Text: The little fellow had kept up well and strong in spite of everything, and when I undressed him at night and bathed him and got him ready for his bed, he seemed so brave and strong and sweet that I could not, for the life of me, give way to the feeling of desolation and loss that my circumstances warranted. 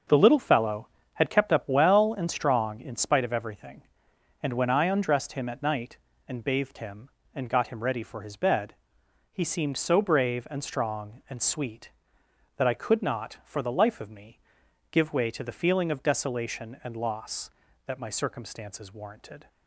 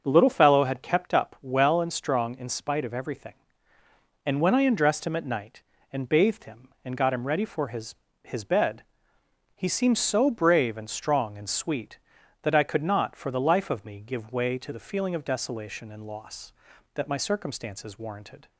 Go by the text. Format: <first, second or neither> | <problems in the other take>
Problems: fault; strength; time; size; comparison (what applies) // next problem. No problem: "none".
first | starts louder than the rest; until 1.0 s; 6.5 dB; noticeable in the first // says "his" twice; at 8.2 s